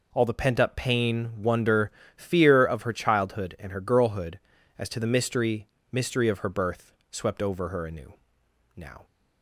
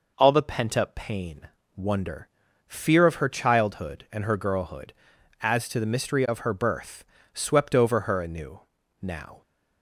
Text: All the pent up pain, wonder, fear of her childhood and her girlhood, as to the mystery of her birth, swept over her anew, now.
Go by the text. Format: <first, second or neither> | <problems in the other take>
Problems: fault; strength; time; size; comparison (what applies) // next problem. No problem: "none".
second | says "mystery" twice; at 5.9 s